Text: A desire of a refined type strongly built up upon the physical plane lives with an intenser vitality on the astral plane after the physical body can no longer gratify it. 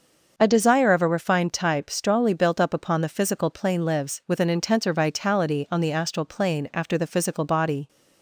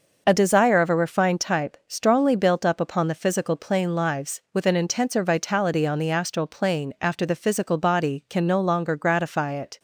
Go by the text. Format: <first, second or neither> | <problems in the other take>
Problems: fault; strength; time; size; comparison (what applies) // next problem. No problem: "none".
second | starts louder than the rest; until 1.3 s; 6.5 dB // stops before "can no longer gratify it"; at 7.8 s